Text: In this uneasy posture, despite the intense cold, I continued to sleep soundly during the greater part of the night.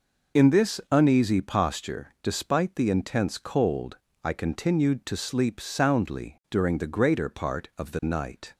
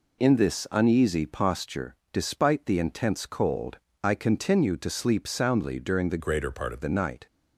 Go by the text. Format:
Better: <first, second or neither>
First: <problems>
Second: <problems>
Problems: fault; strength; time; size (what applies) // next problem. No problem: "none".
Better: first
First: none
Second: changes voice from "greater" to "of"; from 6.1 to 6.8 s; 0.7 s long